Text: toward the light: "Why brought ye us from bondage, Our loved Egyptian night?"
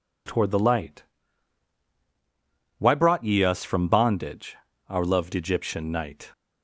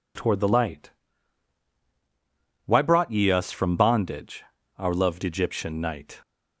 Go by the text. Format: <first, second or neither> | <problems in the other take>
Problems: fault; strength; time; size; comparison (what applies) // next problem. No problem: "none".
neither | none